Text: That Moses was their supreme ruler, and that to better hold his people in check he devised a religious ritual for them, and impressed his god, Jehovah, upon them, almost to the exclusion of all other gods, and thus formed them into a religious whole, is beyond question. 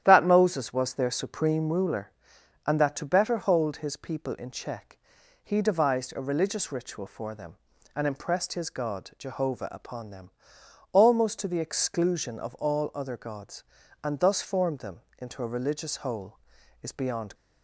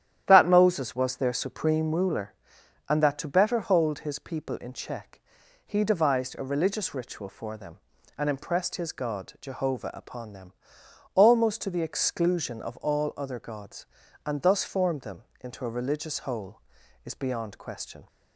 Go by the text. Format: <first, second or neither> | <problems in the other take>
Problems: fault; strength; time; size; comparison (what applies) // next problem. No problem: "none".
second | starts louder than the rest; strong; until 1.0 s; 11 dB; strong in the second // pauses between "check" and "he"; noticeable; at 4.9 s; 0.46 s long; noticeable in the second // pauses between "them" and "into"; slight; at 15.0 s; 0.18 s long; slight in the second // stops before "question"; at 17.3 s